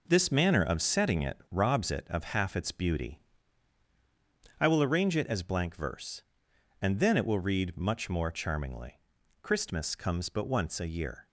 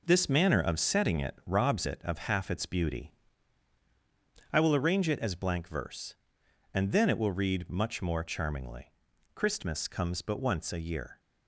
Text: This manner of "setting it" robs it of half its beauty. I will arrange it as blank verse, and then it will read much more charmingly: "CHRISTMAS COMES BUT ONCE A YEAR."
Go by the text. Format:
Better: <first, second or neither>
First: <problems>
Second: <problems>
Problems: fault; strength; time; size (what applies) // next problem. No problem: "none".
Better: neither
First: none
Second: none